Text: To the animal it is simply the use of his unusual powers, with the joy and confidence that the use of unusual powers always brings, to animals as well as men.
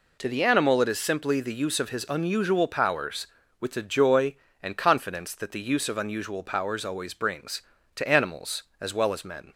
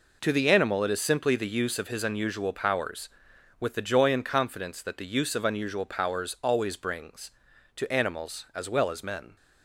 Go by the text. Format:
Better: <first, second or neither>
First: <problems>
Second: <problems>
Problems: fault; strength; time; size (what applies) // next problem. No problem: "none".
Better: neither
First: none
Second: none